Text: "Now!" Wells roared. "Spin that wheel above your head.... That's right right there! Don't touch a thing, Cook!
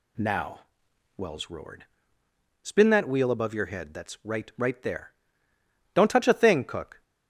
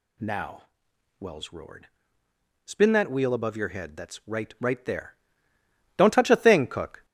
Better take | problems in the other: first | gets louder; noticeable; throughout; 4.5 dB

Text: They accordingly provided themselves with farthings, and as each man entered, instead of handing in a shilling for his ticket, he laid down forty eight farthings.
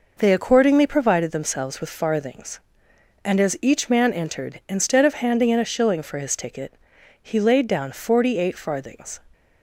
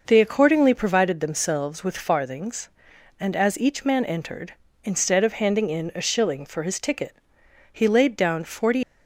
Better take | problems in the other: first | stops before "eight farthings"; at 8.8 s

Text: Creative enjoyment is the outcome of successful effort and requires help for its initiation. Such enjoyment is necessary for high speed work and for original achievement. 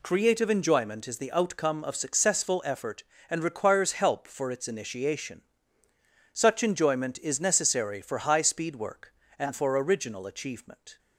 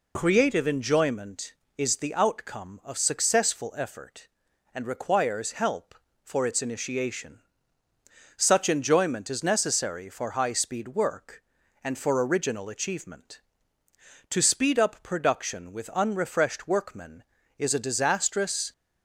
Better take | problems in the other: first | goes on to say "To speed up production with unrefreshed workmen is a disastrous"; strong; from 14.3 s on; 4.4 s long

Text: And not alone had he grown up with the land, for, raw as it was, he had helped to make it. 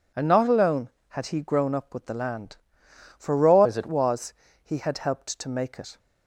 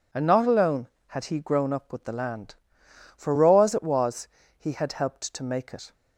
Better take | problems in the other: second | changes voice from "as" to "it"; from 3.6 to 3.8 s; 0.2 s long

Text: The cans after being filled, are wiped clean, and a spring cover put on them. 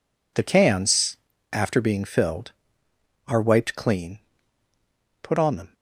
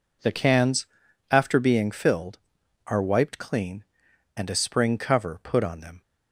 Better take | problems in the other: second | pauses between "cans" and "after"; slight; at 1.1 s; 0.36 s long; noticeable in the second // skips "and a spring cover"; at 4.6 s

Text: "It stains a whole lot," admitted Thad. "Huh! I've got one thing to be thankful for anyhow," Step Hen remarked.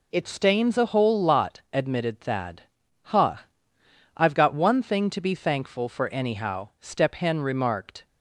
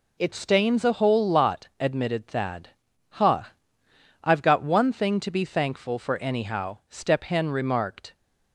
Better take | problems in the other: neither | none

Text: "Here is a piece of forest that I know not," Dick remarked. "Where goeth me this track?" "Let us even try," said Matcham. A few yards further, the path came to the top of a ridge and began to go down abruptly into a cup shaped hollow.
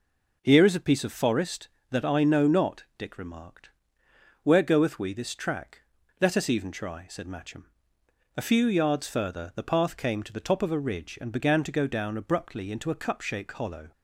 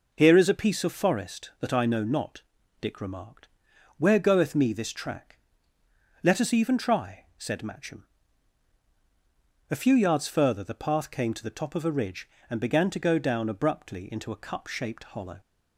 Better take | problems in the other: second | says "we" for "me"; at 4.9 s

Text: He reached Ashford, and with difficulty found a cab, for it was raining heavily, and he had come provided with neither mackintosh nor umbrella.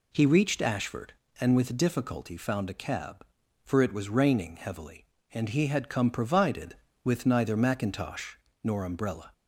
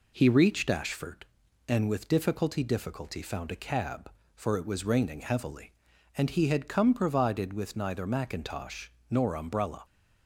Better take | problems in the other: first | says "difficulty" twice; at 2.6 s // pauses between "mackintosh" and "nor"; slight; at 8.8 s; 0.20 s long; slight in the first

